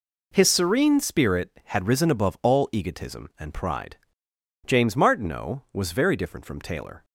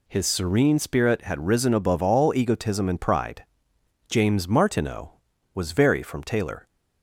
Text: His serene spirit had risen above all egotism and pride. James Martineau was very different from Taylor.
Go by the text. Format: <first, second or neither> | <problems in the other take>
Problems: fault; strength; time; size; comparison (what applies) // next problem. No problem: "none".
first | skips "different"; at 6.0 s